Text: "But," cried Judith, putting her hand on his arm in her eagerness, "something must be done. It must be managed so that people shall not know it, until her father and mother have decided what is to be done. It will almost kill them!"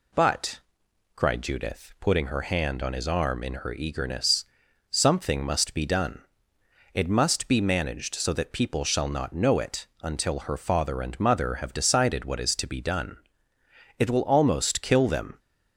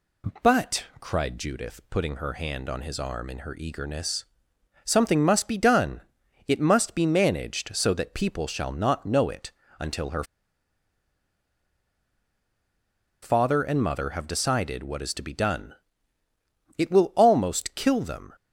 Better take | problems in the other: first | pauses between "her" and "father"; strong; at 10.2 s; 2.9 s long

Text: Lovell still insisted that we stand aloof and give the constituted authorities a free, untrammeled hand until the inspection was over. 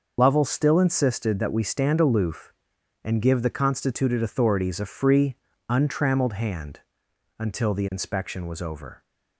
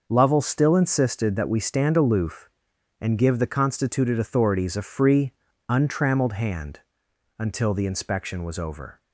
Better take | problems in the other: second | loses the start of "Lovell"; at 0.1 s; 60 ms // starts louder than the rest; until 1.1 s; 6 dB // pauses between "hand" and "until"; noticeable; at 6.8 s; 0.58 s long; noticeable in the second

